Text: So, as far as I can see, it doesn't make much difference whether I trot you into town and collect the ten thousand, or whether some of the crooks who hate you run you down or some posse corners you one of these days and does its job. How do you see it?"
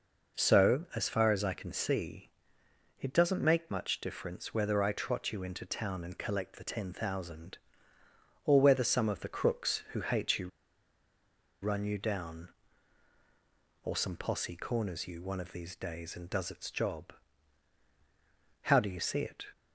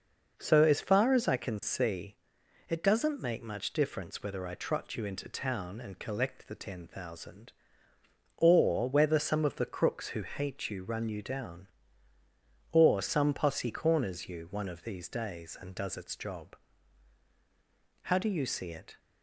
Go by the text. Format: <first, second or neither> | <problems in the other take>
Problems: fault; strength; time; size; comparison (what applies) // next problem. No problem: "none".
second | pauses between "you" and "run"; at 10.4 s; 1.1 s long